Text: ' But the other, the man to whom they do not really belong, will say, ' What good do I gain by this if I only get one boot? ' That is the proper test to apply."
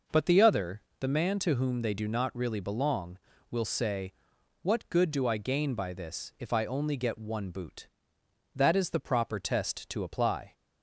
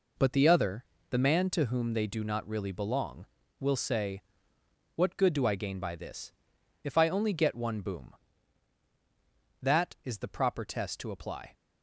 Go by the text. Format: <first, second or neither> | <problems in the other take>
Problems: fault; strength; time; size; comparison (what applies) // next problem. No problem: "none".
first | pauses between "this" and "if"; noticeable; at 6.3 s; 0.52 s long // says "boom" for "boot"; at 7.8 s